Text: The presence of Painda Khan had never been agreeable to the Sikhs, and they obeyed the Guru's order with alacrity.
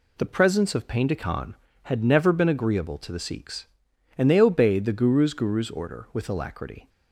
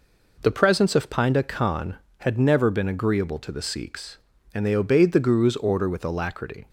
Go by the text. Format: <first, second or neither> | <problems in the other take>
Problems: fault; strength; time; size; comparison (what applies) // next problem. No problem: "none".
second | says "Guru's" twice; at 5.3 s